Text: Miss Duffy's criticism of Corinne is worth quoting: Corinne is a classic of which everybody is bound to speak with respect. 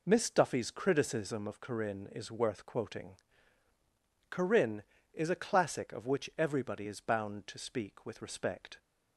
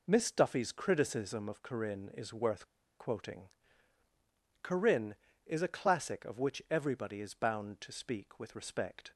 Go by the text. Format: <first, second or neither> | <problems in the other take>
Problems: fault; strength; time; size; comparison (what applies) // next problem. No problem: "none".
first | pauses between "worth" and "quoting"; slight; at 2.6 s; 0.30 s long